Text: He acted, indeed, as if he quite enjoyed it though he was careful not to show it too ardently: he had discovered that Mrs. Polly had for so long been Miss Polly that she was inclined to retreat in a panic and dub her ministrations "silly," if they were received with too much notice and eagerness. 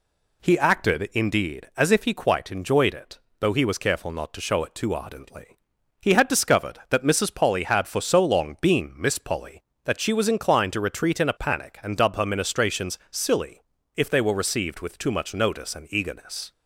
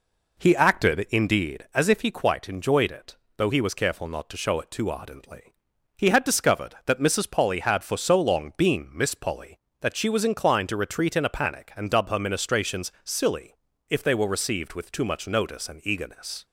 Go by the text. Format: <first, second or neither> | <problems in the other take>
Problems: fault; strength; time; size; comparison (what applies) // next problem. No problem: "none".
first | starts louder than the rest; noticeable; until 1.7 s; 4 dB // pauses between "it" and "though"; slight; at 3.1 s; 0.22 s long; slight in the first